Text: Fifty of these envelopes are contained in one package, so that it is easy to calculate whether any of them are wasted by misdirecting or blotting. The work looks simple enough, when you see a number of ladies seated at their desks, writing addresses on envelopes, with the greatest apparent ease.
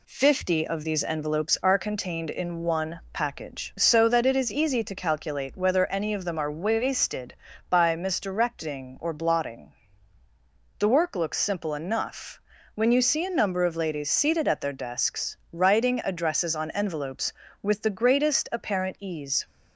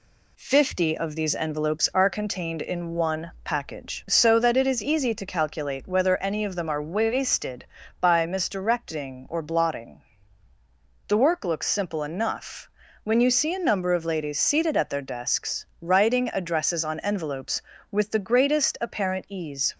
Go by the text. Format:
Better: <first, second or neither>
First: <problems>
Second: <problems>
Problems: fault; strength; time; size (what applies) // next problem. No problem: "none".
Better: neither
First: none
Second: none